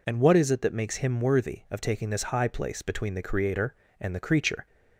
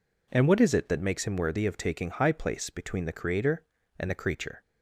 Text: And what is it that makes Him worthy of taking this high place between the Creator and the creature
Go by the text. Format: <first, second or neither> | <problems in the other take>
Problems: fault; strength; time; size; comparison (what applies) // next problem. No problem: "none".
first | skips "this"; at 2.1 s